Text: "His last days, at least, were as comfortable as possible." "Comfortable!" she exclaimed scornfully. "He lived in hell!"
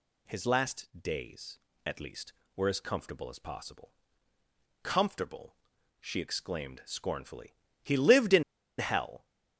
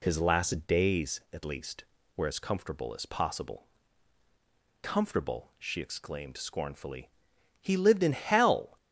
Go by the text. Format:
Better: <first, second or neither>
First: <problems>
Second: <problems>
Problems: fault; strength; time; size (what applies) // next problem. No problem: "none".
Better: second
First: pauses between "in" and "hell"; slight; at 8.4 s; 0.35 s long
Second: none